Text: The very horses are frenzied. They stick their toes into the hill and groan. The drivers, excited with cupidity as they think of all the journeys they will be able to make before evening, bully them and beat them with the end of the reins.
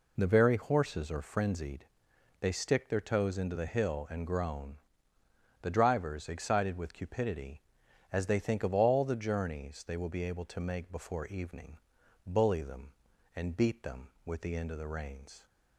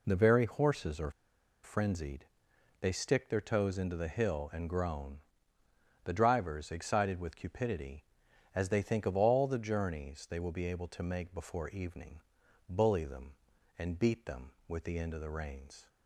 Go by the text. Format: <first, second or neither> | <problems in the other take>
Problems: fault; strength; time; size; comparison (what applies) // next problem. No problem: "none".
first | pauses between "are" and "frenzied"; noticeable; at 1.0 s; 0.54 s long